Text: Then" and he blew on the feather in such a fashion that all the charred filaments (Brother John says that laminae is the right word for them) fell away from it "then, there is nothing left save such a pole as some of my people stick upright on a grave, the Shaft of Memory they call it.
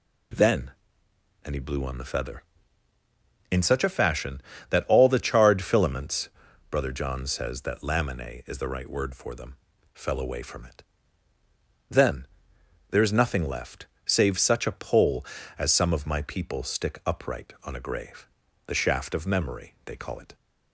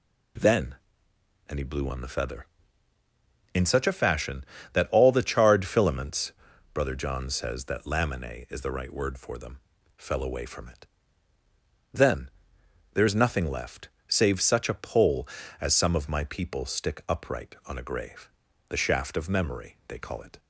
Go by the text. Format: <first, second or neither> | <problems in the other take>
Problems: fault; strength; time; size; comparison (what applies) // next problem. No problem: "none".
neither | pauses between "it" and "then"; the same in both // pauses between "left" and "save"; slight; the same in both